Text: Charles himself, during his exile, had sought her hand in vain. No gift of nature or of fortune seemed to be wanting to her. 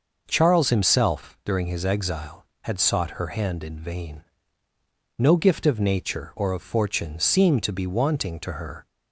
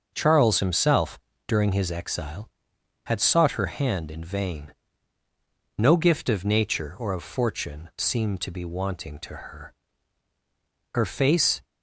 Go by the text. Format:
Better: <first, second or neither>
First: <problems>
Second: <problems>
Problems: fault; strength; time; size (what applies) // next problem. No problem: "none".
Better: first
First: none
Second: starts louder than the rest; until 1.1 s; 6.5 dB // goes on to say "Her face"; noticeable; from 10.9 s on; 0.70 s long